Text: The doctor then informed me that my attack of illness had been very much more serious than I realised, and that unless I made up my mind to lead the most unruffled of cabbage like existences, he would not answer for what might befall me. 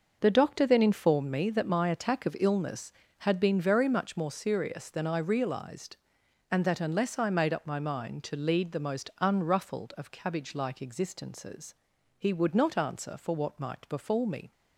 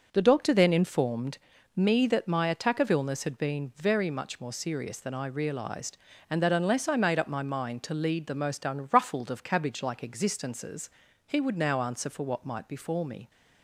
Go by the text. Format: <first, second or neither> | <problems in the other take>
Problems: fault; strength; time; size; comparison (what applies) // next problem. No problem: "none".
first | starts louder than the rest; until 1.1 s; 6.5 dB; noticeable in the first // pauses between "informed" and "me"; at 1.3 s; 0.38 s long // says "now" for "not"; at 11.5 s